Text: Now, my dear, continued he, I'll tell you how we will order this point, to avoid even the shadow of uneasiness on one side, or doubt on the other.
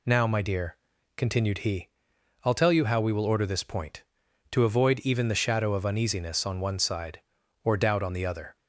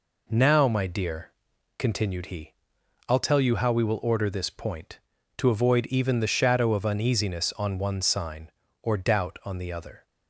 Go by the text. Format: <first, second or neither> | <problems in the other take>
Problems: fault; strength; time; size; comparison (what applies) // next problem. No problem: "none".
first | says "sign" for "side"; at 8.0 s